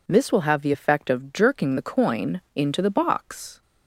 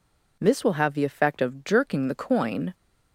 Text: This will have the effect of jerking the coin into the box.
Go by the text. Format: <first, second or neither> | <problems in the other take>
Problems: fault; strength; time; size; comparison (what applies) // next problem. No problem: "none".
first | stops before "into the box"; at 2.7 s